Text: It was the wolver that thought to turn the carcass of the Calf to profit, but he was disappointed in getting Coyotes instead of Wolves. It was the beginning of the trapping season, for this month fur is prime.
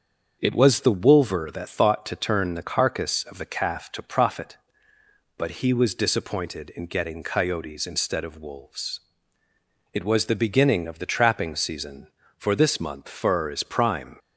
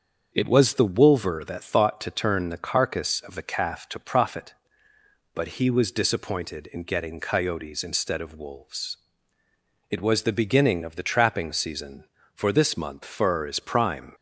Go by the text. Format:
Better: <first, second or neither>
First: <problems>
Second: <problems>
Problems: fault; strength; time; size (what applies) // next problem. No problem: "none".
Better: neither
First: starts louder than the rest; until 1.4 s; 6.5 dB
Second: starts louder than the rest; until 1.3 s; 6.5 dB